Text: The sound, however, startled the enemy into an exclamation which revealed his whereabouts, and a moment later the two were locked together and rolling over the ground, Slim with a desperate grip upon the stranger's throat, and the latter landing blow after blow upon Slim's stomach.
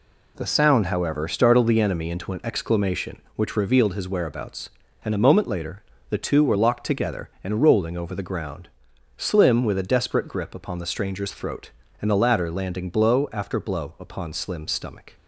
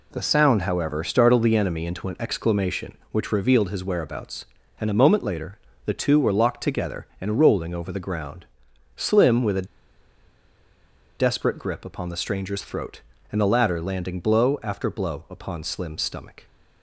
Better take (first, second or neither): first